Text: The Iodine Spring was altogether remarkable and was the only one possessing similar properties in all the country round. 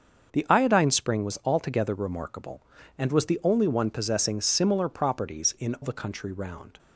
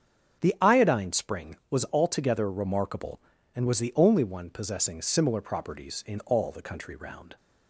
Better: second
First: starts louder than the rest; until 1.3 s; 7 dB // skips "all"; at 5.7 s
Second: starts louder than the rest; strong; until 1.4 s; 8 dB

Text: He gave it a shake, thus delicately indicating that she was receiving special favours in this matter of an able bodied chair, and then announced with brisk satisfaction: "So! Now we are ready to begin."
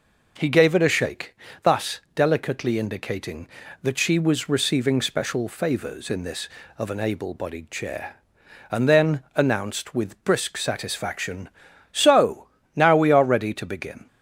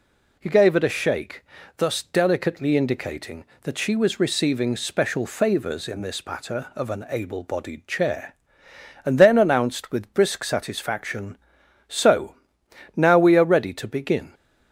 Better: second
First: skips "matter"; at 6.6 s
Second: none

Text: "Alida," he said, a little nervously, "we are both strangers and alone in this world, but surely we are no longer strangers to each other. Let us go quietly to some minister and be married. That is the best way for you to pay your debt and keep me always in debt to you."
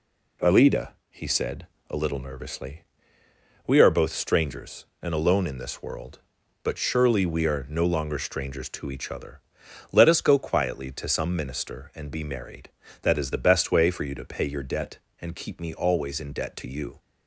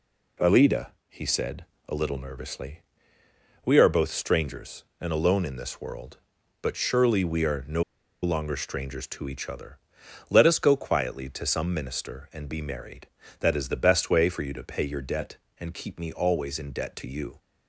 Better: first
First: none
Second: pauses between "no" and "longer"; at 7.8 s; 0.40 s long

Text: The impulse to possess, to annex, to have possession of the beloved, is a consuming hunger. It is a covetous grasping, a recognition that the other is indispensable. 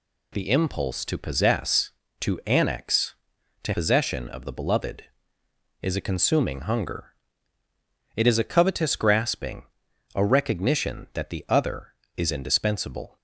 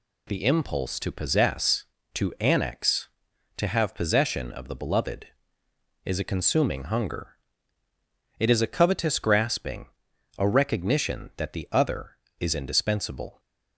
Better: second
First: skips "have"; at 3.7 s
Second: none

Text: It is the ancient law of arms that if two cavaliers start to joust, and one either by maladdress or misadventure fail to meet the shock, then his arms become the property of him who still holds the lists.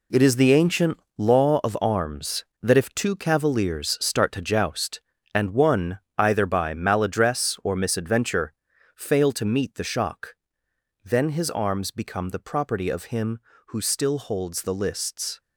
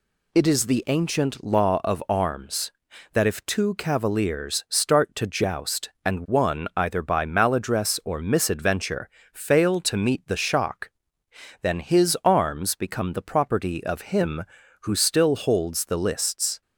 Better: second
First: gets quieter; strong; throughout; 10 dB // pauses between "ancient" and "law"; slight; at 0.9 s; 0.18 s long // pauses between "one" and "either"; slight; at 5.9 s; 0.22 s long // pauses between "misadventure" and "fail"; at 8.5 s; 0.42 s long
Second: pauses between "misadventure" and "fail"; slight; at 9.0 s; 0.22 s long

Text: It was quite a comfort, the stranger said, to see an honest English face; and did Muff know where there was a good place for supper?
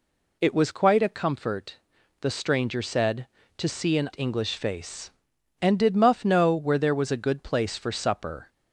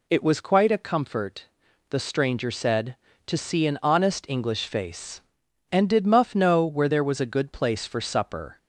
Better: second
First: skips "honest"; at 4.1 s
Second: none

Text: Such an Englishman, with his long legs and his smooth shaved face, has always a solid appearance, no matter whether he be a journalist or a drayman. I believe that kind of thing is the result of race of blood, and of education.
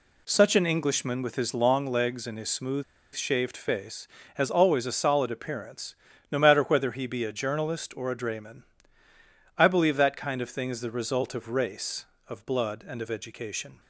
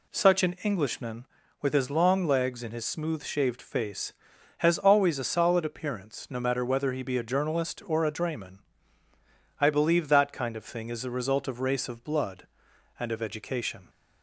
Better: second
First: pauses between "smooth" and "shaved"; slight; at 2.8 s; 0.31 s long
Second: none

